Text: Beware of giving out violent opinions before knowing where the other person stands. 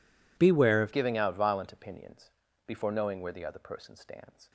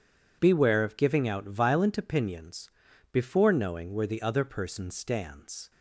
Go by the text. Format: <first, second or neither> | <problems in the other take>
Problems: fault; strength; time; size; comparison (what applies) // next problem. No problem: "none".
second | changes voice at "giving"; from 0.9 s on; 3.6 s long // pauses between "opinions" and "before"; slight; at 2.3 s; 0.34 s long; also in the second